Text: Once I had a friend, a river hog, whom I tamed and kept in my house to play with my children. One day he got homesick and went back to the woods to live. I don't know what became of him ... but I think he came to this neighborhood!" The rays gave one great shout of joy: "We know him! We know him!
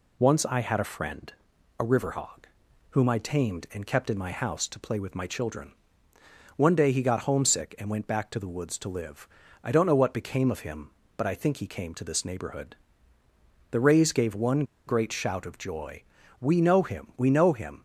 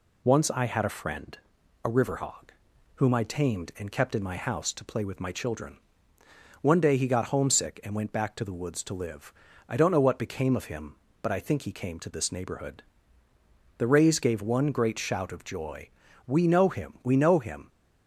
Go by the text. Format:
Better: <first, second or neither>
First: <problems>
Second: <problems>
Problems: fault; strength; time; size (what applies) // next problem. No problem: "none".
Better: second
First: pauses between "one" and "great"; slight; at 14.6 s; 0.23 s long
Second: none